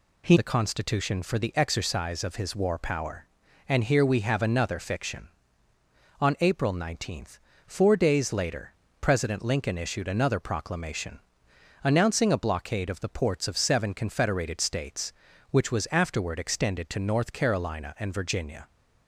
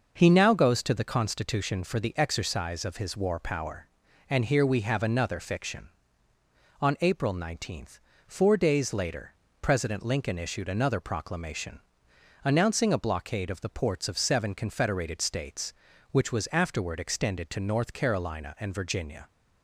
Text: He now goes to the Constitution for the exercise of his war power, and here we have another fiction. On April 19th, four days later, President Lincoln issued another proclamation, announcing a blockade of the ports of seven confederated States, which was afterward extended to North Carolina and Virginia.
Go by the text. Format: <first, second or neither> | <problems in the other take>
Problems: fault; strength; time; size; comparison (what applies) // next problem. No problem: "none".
second | skips "now goes to"; at 0.3 s